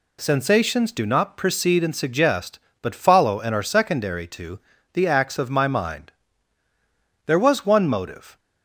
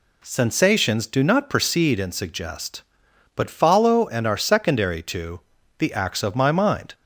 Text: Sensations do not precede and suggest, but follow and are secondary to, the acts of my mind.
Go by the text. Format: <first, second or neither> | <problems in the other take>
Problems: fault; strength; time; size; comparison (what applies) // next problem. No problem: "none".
second | goes on to say "There was one motive"; noticeable; from 7.2 s on; 1.1 s long